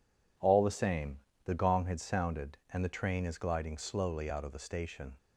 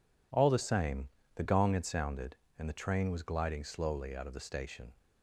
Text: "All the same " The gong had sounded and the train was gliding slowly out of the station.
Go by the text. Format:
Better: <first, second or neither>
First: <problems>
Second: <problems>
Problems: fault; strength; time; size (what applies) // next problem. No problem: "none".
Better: second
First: says "is" for "was"; at 3.2 s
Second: none